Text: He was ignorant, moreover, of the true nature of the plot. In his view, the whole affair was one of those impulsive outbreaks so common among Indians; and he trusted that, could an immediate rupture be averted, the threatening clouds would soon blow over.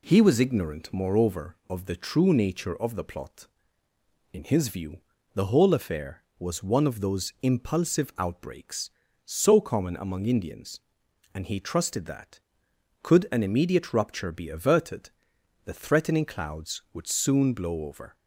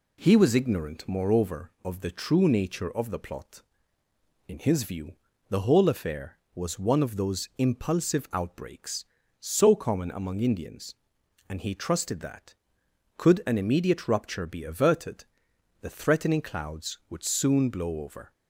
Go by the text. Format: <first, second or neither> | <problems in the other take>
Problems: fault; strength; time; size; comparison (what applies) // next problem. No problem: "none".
neither | none